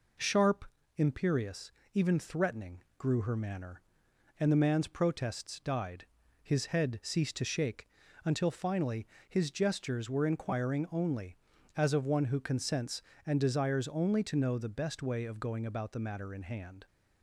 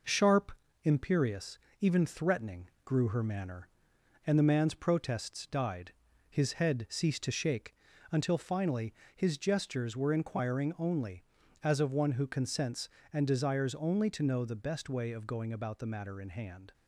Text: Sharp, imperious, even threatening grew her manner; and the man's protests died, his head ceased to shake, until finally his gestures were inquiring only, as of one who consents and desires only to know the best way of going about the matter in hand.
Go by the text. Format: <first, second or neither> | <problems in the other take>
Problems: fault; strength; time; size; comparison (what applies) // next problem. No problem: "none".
first | gets quieter; slight; throughout; 3 dB // pauses between "threatening" and "grew"; slight; at 2.6 s; 0.16 s long; slight in the first // pauses between "finally" and "his"; slight; at 8.9 s; 0.22 s long; slight in the first